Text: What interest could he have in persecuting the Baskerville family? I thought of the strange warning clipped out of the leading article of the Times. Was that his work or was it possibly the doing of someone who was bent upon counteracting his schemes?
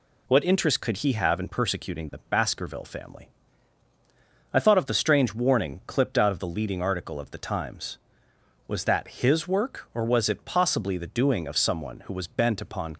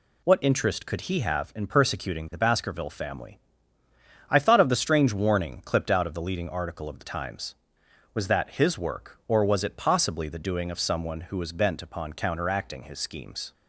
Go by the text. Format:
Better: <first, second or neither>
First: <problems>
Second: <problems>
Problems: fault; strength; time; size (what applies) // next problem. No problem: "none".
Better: second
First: stops before "counteracting his schemes"; at 12.9 s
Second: none